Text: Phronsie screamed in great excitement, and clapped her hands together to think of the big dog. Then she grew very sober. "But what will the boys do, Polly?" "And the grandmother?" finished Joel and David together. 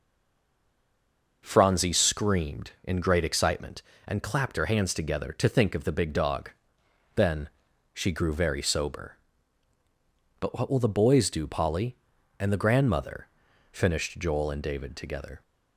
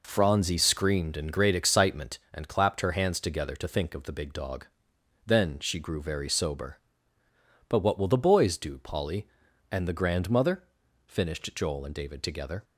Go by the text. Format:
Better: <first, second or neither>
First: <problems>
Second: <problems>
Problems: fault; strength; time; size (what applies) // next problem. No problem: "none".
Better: second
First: stays silent before the first word; noticeable; until 1.4 s; 1.4 s long // pauses between "Then" and "she"; at 7.4 s; 0.42 s long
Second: none